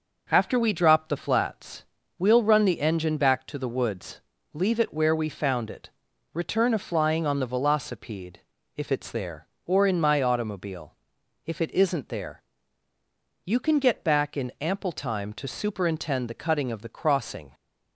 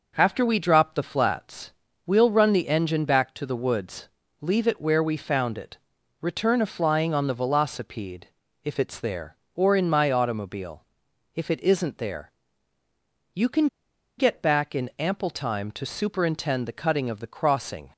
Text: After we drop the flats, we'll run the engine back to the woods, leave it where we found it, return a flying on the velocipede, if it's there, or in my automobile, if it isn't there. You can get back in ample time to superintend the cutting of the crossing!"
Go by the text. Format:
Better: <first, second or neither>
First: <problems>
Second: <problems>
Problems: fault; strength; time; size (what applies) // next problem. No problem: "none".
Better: first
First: none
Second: pauses between "can" and "get"; noticeable; at 13.6 s; 0.51 s long